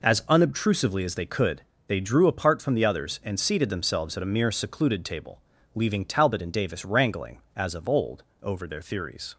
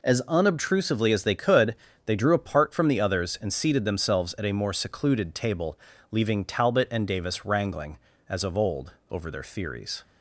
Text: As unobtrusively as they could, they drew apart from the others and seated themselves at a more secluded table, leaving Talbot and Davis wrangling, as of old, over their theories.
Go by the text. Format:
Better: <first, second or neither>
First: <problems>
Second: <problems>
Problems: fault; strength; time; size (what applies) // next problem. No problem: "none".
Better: second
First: says "mere" for "more"; at 4.3 s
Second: none